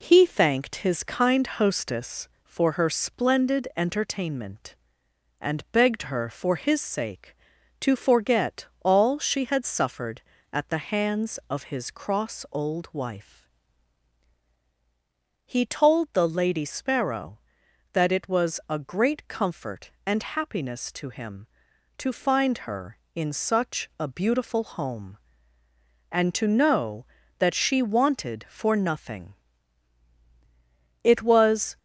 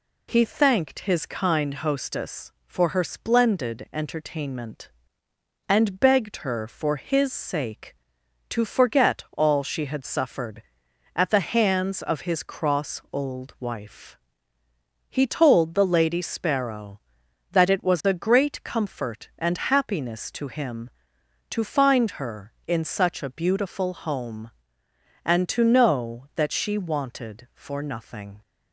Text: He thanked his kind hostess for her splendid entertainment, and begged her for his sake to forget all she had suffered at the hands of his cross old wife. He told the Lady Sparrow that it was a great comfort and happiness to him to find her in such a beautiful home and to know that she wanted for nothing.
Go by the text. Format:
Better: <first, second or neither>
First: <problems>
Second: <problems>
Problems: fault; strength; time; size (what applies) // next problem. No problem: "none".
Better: second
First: pauses between "forget" and "all"; slight; at 8.6 s; 0.18 s long // goes on to say "It was"; noticeable; from 31.0 s on; 0.76 s long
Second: none